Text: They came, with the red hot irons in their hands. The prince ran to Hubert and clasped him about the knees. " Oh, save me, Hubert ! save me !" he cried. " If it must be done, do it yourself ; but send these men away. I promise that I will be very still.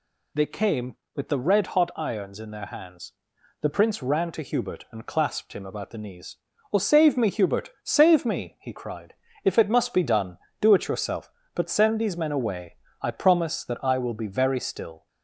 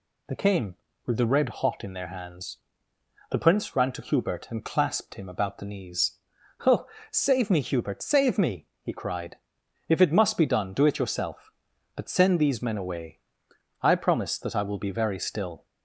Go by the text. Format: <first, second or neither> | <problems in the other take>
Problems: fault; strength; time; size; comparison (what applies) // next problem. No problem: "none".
first | skips "irons"; at 1.8 s